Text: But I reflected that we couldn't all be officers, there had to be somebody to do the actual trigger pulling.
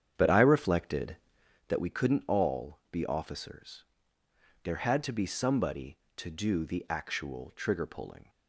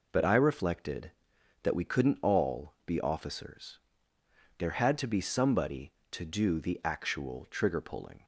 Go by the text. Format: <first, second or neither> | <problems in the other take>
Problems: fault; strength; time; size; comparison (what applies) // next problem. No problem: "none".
second | starts louder than the rest; strong; until 1.7 s; 8.5 dB